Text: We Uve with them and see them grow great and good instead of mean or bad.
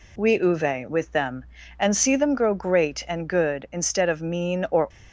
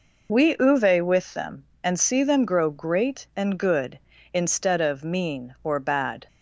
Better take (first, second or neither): second